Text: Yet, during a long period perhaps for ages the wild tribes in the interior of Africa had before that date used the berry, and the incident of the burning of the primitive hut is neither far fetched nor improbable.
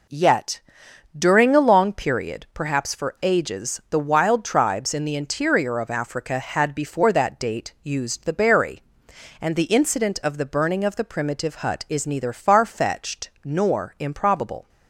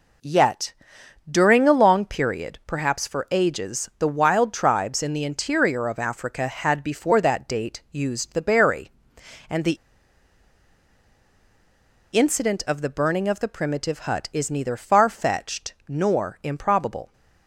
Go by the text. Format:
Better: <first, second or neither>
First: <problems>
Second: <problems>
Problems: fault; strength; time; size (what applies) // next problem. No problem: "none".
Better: first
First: none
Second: pauses between "the" and "incident"; strong; at 9.7 s; 2.3 s long